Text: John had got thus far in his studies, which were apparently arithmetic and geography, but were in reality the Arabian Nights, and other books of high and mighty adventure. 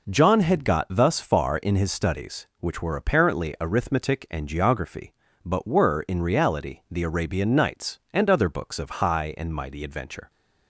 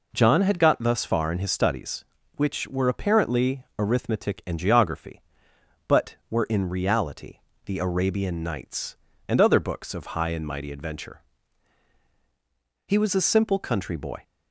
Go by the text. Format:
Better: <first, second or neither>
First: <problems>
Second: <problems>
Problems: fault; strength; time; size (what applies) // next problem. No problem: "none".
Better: first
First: none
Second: pauses between "reality" and "the"; slight; at 7.3 s; 0.28 s long // goes on to say "He was a simple country boy"; from 12.8 s on; 1.3 s long